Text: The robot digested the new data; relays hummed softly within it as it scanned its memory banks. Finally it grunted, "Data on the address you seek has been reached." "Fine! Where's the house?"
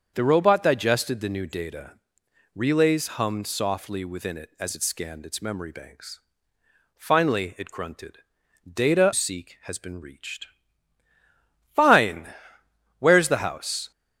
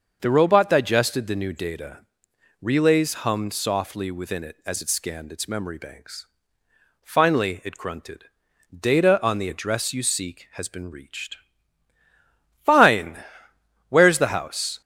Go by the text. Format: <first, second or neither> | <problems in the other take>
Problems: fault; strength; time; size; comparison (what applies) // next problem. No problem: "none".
second | starts louder than the rest; until 1.1 s; 7 dB; also in the second // skips "on the address you"; at 9.1 s